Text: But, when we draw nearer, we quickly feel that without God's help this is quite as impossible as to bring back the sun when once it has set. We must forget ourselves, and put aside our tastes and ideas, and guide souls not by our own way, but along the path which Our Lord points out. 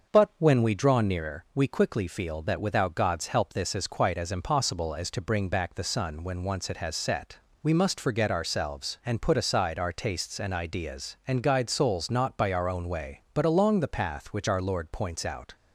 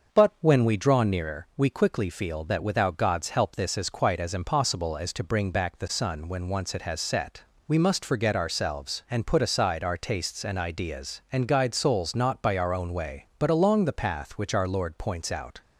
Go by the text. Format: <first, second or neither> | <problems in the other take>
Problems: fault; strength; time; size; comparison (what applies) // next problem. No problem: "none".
neither | starts louder than the rest; the same in both